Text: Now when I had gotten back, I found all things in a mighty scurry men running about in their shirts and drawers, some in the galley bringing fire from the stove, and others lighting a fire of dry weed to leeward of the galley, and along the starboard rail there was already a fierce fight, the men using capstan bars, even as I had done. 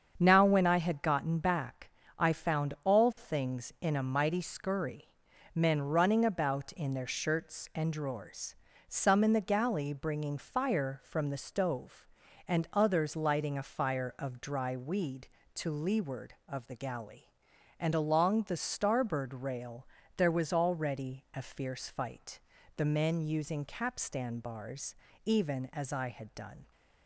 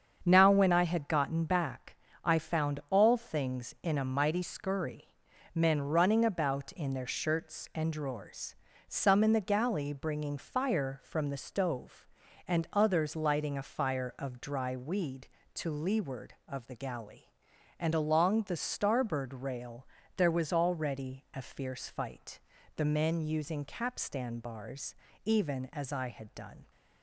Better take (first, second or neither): neither